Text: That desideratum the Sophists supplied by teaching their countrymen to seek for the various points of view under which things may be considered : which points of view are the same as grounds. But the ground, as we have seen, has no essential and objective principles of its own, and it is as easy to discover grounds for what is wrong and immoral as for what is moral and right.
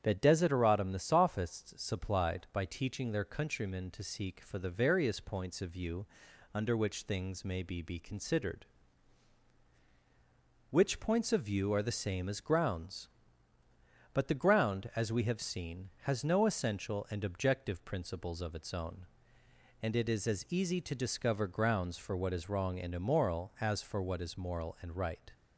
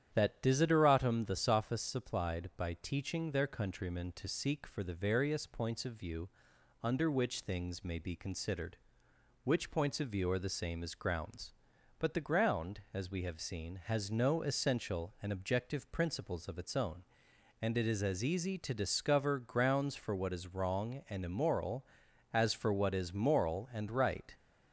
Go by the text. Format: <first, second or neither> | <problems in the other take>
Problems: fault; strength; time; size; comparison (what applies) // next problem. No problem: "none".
second | starts louder than the rest; strong; until 1.0 s; 9 dB; strong in the second // pauses between "view" and "under"; noticeable; at 6.0 s; 0.48 s long; noticeable in the second // says "be" twice; at 7.8 s